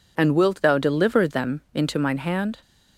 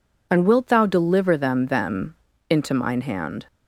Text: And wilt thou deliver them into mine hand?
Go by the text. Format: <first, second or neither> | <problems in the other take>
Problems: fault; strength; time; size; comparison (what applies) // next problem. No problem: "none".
first | says "them" twice; at 1.6 s